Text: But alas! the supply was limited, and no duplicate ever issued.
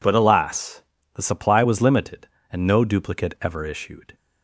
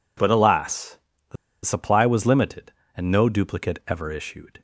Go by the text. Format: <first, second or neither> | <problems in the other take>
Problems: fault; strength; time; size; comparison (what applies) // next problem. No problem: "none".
first | pauses between "the" and "supply"; slight; at 1.3 s; 0.29 s long